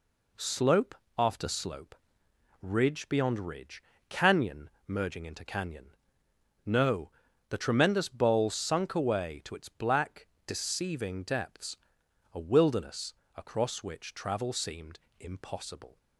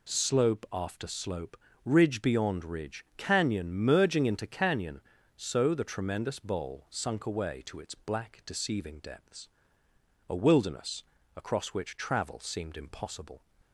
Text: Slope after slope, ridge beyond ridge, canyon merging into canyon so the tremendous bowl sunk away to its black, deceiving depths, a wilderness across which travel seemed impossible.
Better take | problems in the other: second | pauses between "Slope" and "after"; slight; at 0.9 s; 0.24 s long // pauses between "canyon" and "merging"; slight; at 4.6 s; 0.18 s long // says "no" for "so"; at 6.6 s // pauses between "wilderness" and "across"; slight; at 13.1 s; 0.24 s long; slight in the second // pauses between "seemed" and "impossible"; slight; at 14.9 s; 0.20 s long

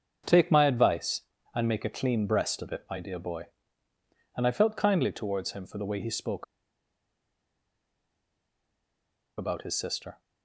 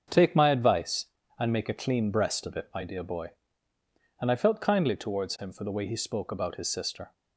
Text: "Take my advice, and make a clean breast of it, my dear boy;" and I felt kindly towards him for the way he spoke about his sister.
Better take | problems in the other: second | starts louder than the rest; until 1.5 s; 7 dB; also in the second // pauses between "spoke" and "about"; strong; at 6.4 s; 2.9 s long

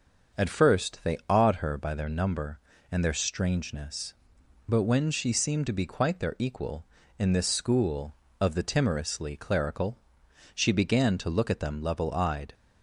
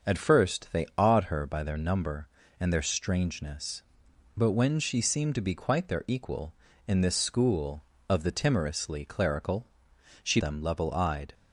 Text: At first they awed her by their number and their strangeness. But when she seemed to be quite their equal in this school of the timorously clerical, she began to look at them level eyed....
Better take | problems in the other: first | starts louder than the rest; until 1.1 s; 6.5 dB; also in the first // skips "began to look at"; at 10.3 s

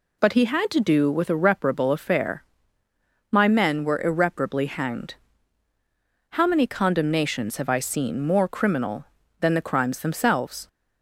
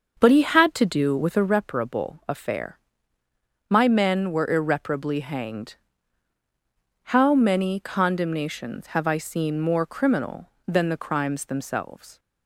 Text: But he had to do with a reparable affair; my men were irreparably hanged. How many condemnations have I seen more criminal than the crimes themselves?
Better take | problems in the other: first | starts louder than the rest; until 1.5 s; 6.5 dB

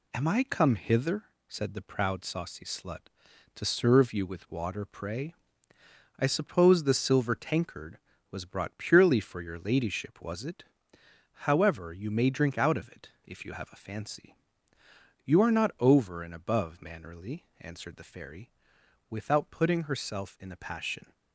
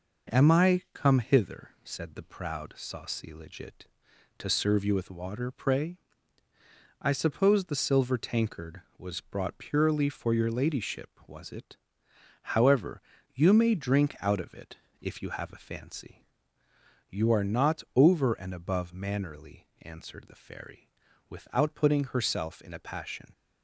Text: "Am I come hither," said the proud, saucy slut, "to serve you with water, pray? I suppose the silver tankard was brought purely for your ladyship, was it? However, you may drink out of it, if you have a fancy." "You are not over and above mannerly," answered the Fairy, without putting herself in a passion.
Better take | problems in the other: first | says "legit" for "slut"; at 3.3 s

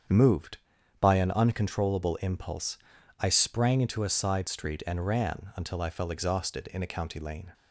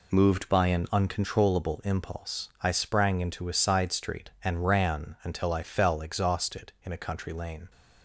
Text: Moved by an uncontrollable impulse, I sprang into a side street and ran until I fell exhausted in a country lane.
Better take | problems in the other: second | starts louder than the rest; strong; until 1.5 s; 7.5 dB // says "county" for "country"; at 6.8 s

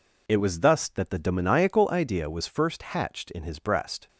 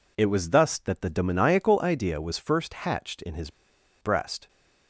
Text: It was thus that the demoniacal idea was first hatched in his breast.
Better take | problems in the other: first | pauses between "his" and "breast"; noticeable; at 3.4 s; 0.51 s long

